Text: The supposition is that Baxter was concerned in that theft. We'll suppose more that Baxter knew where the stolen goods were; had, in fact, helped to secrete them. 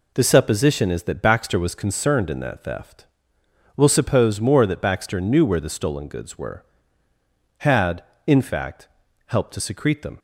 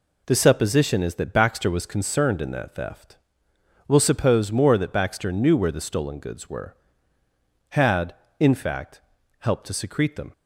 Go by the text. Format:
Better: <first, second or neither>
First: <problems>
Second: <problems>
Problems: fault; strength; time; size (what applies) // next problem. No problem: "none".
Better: neither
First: none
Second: none